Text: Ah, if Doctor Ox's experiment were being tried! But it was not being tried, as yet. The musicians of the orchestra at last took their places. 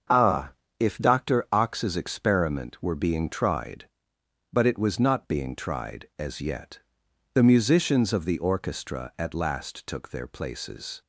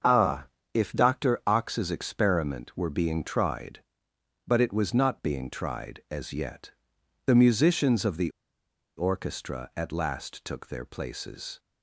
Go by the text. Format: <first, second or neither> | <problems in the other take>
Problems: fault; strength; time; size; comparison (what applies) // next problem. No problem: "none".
first | starts louder than the rest; until 1.3 s; 7 dB; also in the first // pauses between "the" and "orchestra"; noticeable; at 8.2 s; 0.68 s long